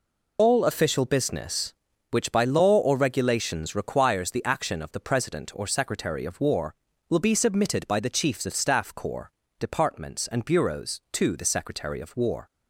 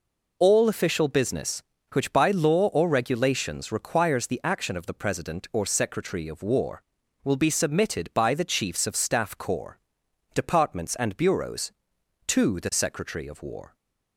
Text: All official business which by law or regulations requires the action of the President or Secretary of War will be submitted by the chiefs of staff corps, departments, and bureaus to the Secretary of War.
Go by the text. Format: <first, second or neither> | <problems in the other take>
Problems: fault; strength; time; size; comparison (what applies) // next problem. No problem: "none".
second | loses the start of "All"; at 0.3 s; 105 ms